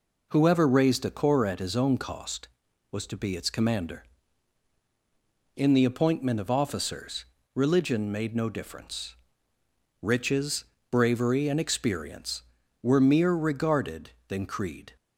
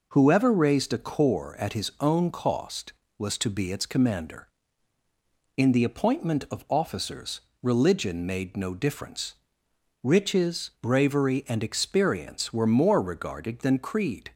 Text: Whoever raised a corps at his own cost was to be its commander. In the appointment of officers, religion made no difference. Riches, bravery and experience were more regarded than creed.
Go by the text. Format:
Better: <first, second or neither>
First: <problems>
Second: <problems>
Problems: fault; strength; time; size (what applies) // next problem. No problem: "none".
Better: second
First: says "mere" for "more"; at 13.0 s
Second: none